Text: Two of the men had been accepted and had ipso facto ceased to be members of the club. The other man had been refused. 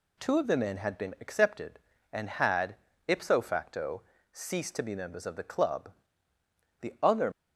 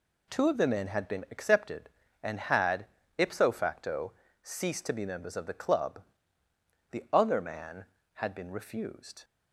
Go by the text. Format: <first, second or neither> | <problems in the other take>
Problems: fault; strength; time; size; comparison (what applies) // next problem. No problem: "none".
second | pauses between "had" and "ipso"; slight; at 2.7 s; 0.30 s long; slight in the second // pauses between "facto" and "ceased"; slight; at 4.0 s; 0.30 s long; slight in the second // stops before "man had been refused"; at 7.3 s